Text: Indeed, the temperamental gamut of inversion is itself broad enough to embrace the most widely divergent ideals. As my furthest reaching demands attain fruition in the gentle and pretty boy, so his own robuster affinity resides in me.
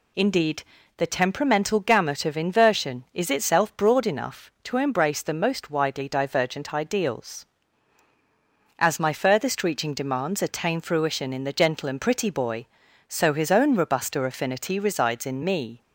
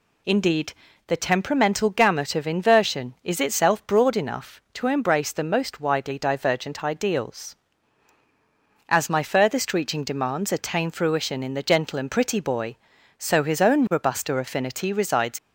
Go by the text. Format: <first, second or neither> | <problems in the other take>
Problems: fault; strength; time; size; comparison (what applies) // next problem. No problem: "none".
first | stops before "in me"; at 15.3 s